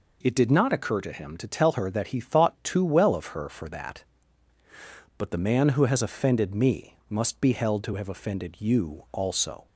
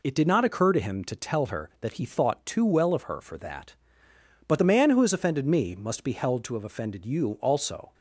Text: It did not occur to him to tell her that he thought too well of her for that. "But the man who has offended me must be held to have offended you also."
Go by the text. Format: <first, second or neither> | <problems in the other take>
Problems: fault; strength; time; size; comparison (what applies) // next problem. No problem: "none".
neither | none